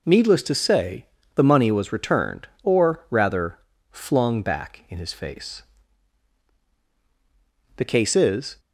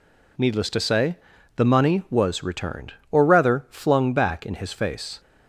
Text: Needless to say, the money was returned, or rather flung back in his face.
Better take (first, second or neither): second